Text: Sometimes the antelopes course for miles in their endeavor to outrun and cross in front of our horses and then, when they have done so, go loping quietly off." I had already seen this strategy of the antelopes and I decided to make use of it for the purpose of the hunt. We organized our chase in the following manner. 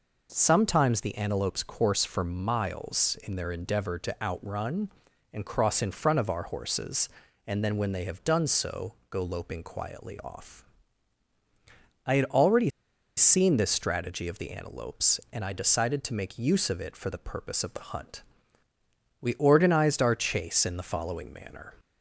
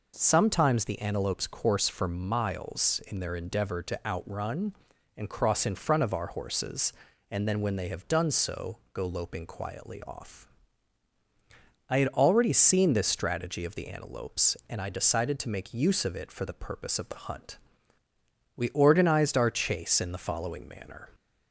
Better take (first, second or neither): second